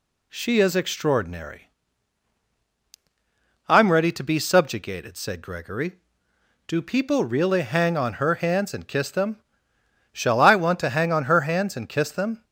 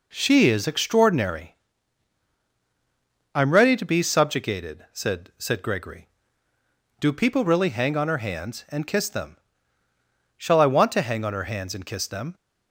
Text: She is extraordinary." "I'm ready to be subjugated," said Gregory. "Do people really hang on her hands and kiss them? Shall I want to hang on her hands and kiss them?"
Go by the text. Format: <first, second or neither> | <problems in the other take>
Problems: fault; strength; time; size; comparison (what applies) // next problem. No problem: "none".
first | says "said" twice; at 5.3 s